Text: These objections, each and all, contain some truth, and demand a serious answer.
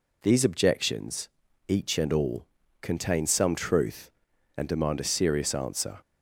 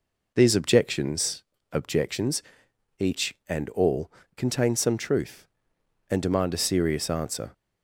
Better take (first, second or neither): first